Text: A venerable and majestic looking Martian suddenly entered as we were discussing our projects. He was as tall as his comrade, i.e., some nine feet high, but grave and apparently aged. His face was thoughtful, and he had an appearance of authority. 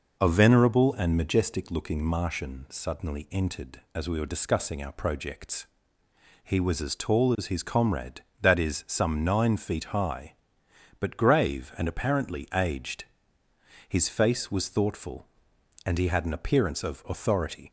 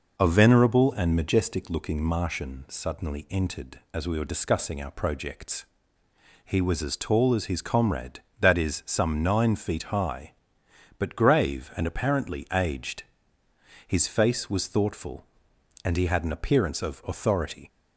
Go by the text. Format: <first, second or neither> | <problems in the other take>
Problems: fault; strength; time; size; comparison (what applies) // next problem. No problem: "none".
neither | none